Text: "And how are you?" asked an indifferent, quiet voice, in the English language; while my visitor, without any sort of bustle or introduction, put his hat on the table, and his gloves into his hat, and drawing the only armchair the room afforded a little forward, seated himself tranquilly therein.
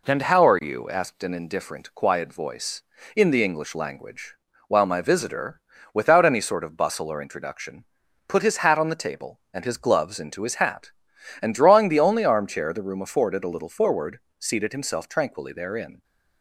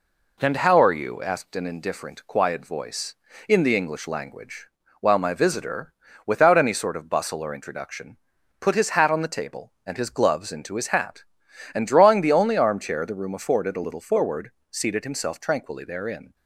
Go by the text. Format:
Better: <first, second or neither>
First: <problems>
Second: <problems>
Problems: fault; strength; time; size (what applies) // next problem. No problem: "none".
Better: neither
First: none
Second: none